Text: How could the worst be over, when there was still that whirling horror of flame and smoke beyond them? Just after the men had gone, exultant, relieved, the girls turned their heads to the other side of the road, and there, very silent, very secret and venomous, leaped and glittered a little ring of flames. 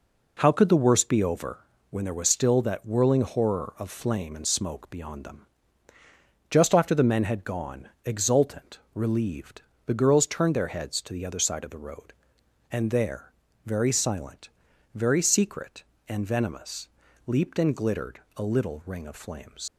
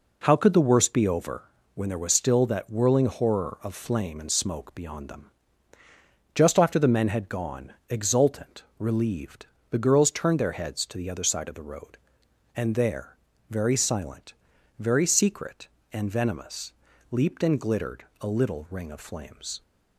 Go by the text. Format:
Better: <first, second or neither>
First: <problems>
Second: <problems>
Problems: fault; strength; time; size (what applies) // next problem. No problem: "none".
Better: second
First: pauses between "glittered" and "a"; slight; at 18.1 s; 0.16 s long // leaves "flames" unfinished; at 19.6 s; 100 ms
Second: pauses between "glittered" and "a"; slight; at 18.0 s; 0.16 s long